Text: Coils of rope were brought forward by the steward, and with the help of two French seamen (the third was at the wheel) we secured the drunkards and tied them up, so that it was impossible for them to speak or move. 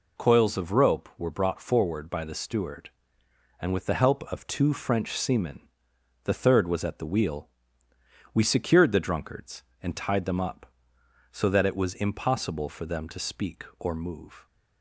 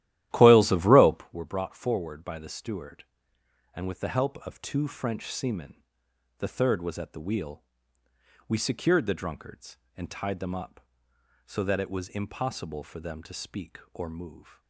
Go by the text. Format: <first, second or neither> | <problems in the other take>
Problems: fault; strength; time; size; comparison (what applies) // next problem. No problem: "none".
first | starts louder than the rest; strong; until 1.4 s; 13.5 dB